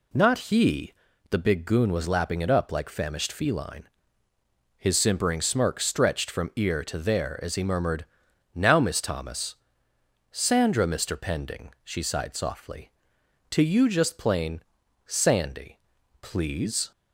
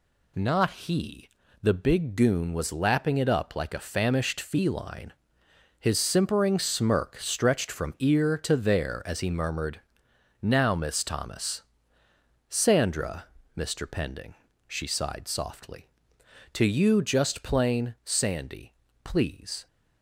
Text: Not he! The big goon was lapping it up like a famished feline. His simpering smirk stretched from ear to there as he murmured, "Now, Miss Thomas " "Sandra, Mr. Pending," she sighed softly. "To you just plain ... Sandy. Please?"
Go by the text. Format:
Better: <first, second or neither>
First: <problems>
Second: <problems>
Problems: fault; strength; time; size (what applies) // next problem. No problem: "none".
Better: second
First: skips "a"; at 2.8 s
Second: none